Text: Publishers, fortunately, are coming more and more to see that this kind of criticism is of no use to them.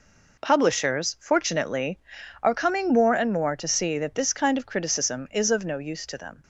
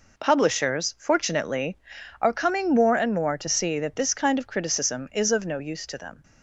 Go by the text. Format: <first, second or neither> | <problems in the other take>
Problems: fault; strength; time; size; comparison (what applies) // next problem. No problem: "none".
neither | none